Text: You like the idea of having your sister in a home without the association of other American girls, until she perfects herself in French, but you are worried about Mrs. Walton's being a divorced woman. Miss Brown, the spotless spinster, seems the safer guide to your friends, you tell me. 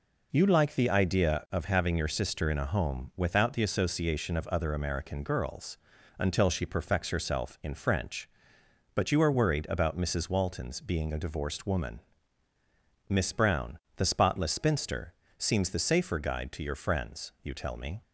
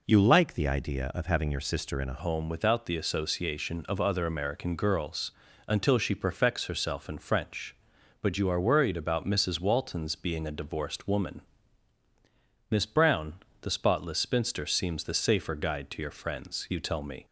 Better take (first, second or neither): first